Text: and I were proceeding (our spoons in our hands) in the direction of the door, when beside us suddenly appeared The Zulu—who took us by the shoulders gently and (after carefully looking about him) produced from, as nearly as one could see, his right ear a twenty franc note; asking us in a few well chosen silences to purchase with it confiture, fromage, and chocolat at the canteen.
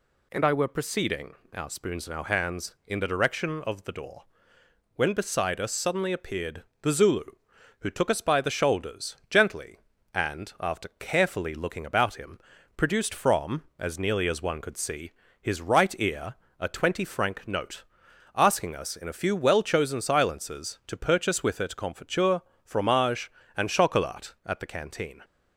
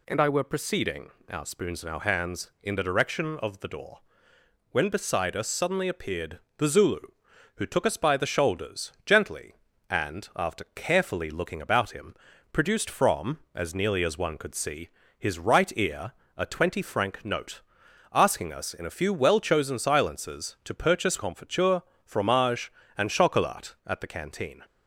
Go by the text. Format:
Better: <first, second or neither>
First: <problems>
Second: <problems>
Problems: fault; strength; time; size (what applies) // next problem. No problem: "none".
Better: first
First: pauses between "appeared" and "The"; slight; at 6.6 s; 0.20 s long // pauses between "ear" and "a"; slight; at 16.3 s; 0.24 s long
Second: pauses between "appeared" and "The"; slight; at 6.3 s; 0.20 s long // pauses between "ear" and "a"; slight; at 16.1 s; 0.24 s long // skips "with it"; at 21.1 s